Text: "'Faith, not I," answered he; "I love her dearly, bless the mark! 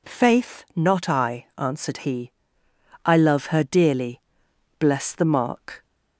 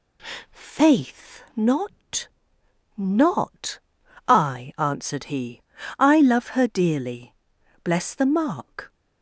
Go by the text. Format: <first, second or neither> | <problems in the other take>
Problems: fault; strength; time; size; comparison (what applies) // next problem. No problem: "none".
first | says "not" twice; at 2.9 s